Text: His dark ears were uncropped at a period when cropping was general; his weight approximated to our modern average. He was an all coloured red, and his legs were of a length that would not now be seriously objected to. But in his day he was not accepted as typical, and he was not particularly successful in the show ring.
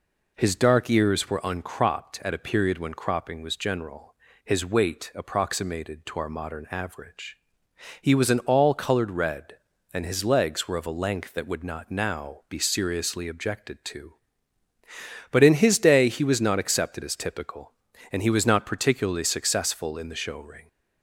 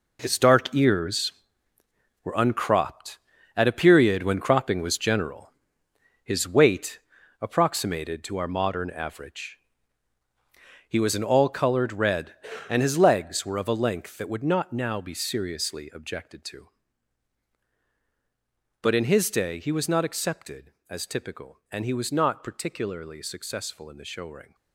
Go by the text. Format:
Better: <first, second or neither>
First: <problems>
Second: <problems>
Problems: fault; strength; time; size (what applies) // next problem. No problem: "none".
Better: first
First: none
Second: gets quieter; strong; throughout; 11 dB // pauses between "weight" and "approximated"; at 6.9 s; 0.42 s long